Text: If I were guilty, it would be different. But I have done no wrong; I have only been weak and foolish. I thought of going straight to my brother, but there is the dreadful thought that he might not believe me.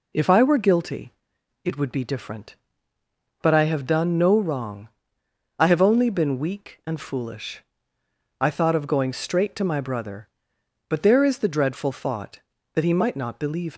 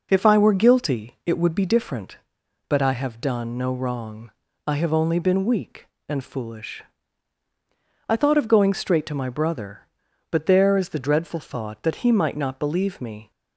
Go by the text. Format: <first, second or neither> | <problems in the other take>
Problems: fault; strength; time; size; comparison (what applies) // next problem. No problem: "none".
second | stops before "me"; at 13.7 s